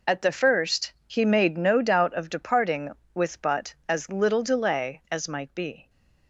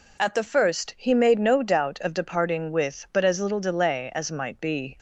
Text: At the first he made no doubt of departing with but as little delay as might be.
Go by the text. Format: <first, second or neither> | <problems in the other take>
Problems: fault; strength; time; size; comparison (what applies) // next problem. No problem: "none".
second | gets quieter; strong; throughout; 12.5 dB